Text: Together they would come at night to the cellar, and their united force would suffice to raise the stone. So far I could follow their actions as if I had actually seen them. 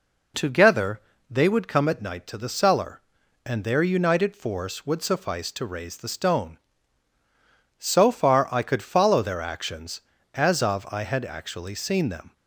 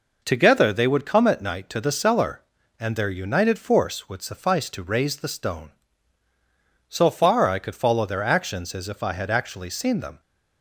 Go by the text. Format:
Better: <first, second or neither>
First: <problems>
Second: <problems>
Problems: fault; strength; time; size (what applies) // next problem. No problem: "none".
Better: second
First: pauses between "Together" and "they"; slight; at 0.9 s; 0.30 s long // says "of" for "if"; at 10.6 s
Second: none